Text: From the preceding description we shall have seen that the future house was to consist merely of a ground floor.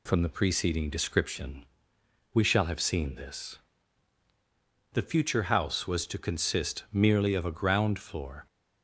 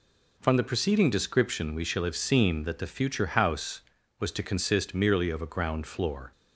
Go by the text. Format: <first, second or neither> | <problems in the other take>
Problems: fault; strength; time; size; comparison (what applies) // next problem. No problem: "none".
second | pauses between "description" and "we"; noticeable; at 1.6 s; 0.68 s long // says "this" for "that"; at 3.1 s